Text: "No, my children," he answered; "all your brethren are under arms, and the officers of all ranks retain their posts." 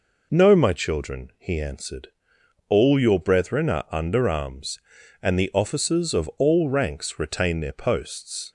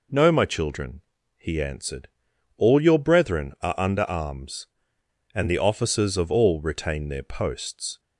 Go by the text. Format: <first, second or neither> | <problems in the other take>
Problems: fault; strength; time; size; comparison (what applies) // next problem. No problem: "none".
first | skips "ranks"; at 6.6 s